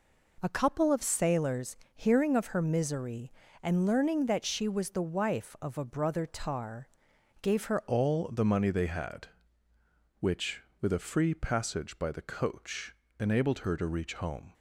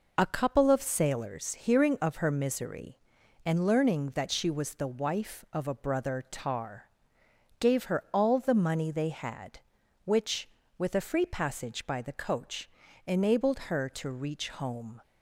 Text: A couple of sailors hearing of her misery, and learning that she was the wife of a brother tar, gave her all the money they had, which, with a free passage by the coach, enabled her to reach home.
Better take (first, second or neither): second